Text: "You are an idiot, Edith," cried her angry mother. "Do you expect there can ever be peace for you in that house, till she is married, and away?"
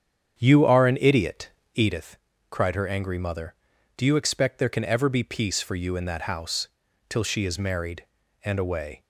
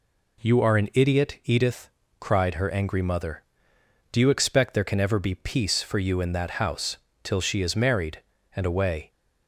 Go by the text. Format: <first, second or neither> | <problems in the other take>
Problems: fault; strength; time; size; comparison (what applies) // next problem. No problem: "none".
second | starts louder than the rest; strong; until 2.1 s; 8 dB